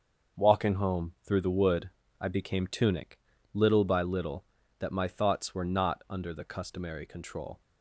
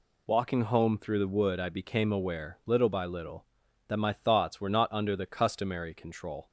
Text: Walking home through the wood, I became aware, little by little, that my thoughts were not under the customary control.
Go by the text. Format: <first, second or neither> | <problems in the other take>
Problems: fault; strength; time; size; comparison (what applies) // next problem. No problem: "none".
second | starts louder than the rest; until 1.5 s; 6.5 dB // says "tunic" for "aware"; at 2.6 s